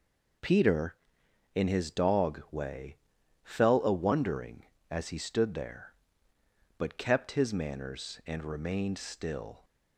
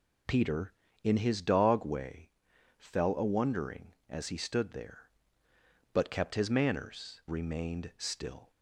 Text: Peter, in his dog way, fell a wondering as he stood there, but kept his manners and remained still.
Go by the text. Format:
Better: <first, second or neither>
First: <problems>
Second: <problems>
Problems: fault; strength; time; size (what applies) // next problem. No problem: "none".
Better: first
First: none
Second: skips "and"; at 7.2 s